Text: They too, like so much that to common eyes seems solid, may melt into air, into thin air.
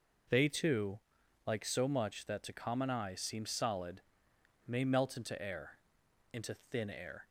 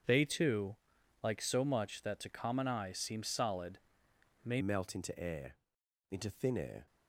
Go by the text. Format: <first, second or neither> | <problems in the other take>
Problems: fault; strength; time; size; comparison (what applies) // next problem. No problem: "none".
first | starts louder than the rest; strong; until 1.5 s; 7.5 dB // changes voice at "melt"; from 4.5 s on; 2.3 s long